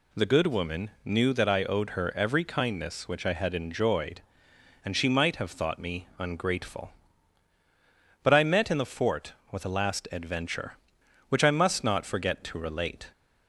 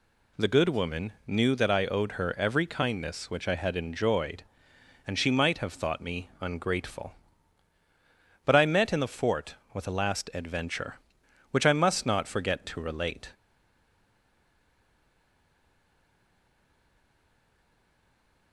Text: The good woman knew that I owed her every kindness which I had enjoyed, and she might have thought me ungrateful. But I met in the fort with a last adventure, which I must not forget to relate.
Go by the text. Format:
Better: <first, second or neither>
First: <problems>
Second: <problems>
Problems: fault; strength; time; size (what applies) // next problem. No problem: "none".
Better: first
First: pauses between "woman" and "knew"; slight; at 0.8 s; 0.16 s long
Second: pauses between "woman" and "knew"; slight; at 1.1 s; 0.16 s long // stays silent after the last word; strong; from 13.3 s on; 5.2 s long